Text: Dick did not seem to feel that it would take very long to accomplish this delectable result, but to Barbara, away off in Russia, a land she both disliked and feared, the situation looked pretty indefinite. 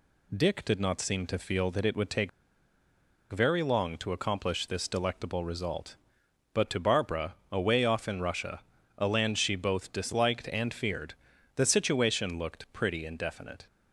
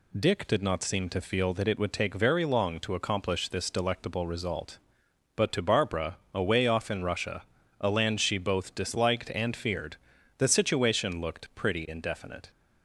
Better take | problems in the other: second | pauses between "take" and "very"; at 2.2 s; 1.0 s long

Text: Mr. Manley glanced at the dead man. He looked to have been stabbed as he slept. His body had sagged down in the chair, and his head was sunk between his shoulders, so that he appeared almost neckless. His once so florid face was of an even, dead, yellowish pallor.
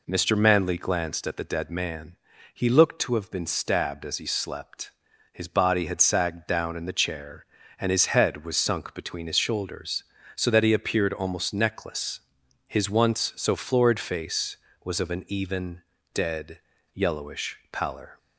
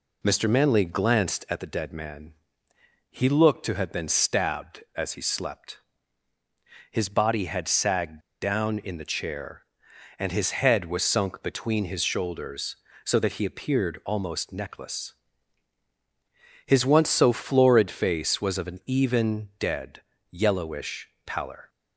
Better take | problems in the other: first | pauses between "sagged" and "down"; slight; at 8.2 s; 0.20 s long // pauses between "yellowish" and "pallor"; slight; at 21.0 s; 0.16 s long

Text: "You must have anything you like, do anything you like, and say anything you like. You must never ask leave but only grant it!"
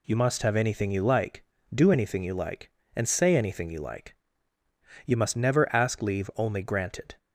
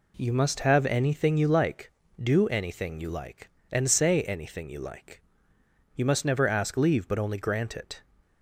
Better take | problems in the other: second | skips "but"; at 6.3 s

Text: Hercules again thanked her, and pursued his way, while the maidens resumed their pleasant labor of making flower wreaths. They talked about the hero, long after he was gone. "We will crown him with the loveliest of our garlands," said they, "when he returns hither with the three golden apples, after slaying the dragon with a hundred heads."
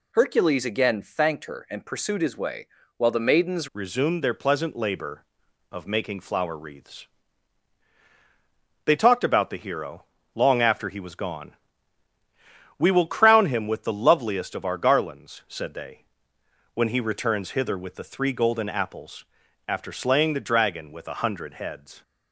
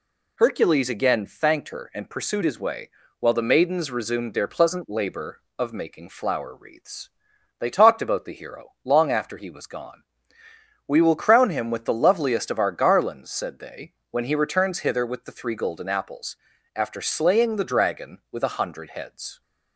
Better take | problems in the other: second | changes voice at "resumed"; from 3.7 s on; 18.3 s long

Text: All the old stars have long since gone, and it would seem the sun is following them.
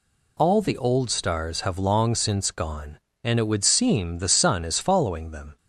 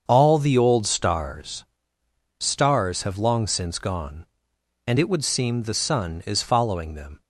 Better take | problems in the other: first | starts louder than the rest; until 1.0 s; 7 dB // says "stars" twice; at 2.3 s

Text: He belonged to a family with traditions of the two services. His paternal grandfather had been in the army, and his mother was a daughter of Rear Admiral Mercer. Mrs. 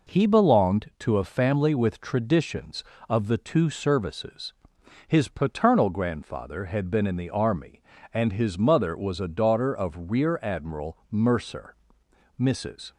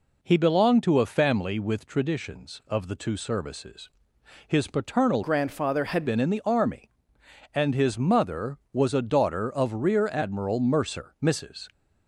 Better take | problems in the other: first | changes voice from "grandfather" to "had"; from 5.2 to 6.0 s; 0.8 s long

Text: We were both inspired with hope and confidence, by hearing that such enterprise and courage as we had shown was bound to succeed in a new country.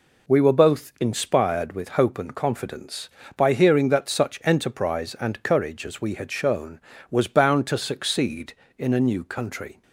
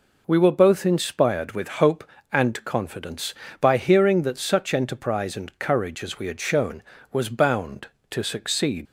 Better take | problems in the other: first | stops before "in a new country"; at 8.8 s

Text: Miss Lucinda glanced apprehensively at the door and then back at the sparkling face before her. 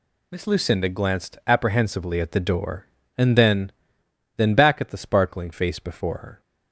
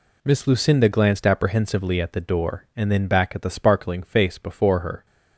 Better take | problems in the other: second | says "then" twice; at 4.3 s

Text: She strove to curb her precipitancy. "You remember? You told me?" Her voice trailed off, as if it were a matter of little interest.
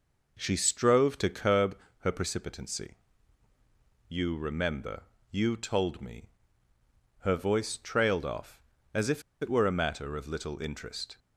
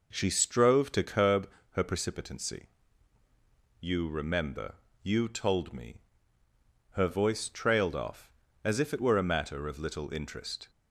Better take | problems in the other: second | pauses between "curb" and "her"; slight; at 1.7 s; 0.26 s long; slight in the second // pauses between "if" and "it"; slight; at 9.2 s; 0.20 s long

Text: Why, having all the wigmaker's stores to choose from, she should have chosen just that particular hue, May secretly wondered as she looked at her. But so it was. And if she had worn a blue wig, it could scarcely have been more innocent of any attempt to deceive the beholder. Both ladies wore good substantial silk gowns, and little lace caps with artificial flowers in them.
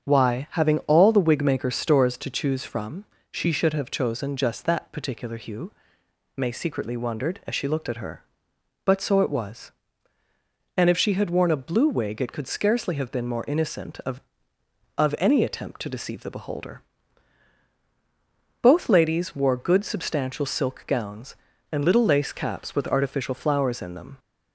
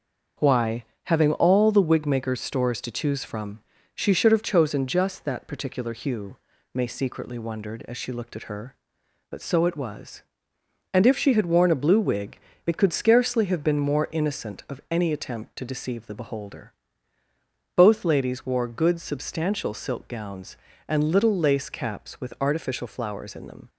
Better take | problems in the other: second | starts louder than the rest; strong; until 1.0 s; 7.5 dB; also in the second // says "of" twice; at 14.9 s

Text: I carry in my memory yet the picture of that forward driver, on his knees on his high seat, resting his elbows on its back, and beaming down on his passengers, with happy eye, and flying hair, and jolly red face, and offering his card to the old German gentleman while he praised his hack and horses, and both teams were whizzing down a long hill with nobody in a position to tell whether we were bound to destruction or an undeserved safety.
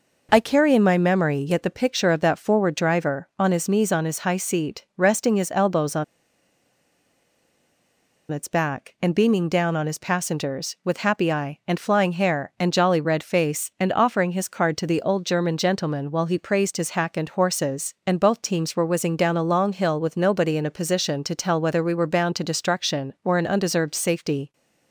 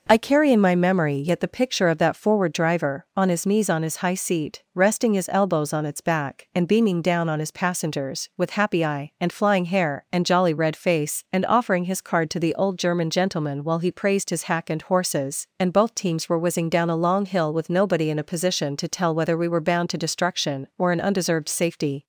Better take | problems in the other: second | pauses between "on" and "its"; strong; at 6.0 s; 2.2 s long

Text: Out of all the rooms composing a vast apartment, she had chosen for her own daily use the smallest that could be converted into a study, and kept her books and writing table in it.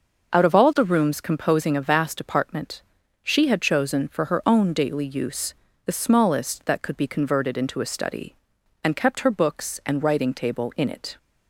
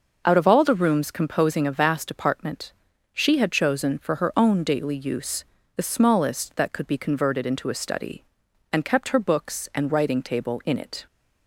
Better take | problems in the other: neither | pauses between "use" and "the"; slight; the same in both

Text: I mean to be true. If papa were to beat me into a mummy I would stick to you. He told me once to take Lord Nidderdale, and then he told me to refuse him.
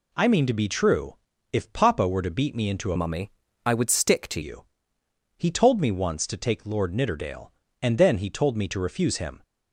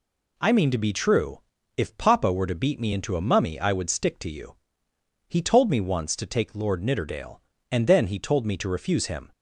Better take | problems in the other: second | changes voice from "mummy" to "to"; from 2.9 to 4.4 s; 1.5 s long // pauses between "mummy" and "I"; slight; at 3.3 s; 0.34 s long

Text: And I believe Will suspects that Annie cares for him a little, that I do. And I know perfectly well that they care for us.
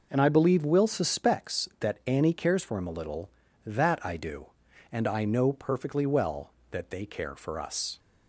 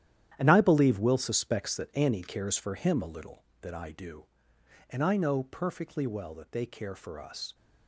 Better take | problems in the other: first | gets quieter; strong; throughout; 11.5 dB

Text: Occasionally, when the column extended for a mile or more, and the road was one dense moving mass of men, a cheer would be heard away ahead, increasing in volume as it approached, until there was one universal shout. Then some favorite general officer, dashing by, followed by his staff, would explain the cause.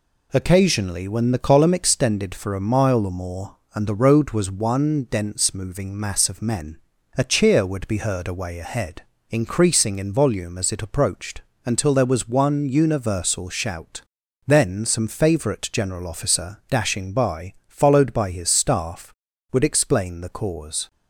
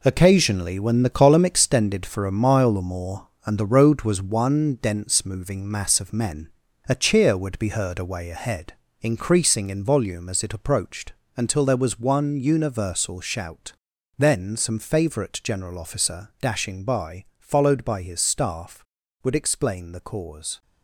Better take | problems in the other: first | gets quieter; strong; throughout; 9 dB

